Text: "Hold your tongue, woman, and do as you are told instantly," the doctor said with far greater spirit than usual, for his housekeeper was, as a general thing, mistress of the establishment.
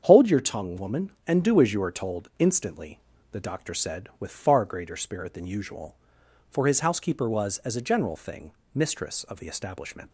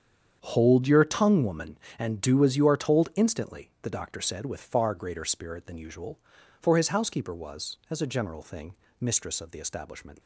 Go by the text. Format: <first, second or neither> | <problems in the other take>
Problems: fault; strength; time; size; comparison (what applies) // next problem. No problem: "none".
neither | starts louder than the rest; strong; the same in both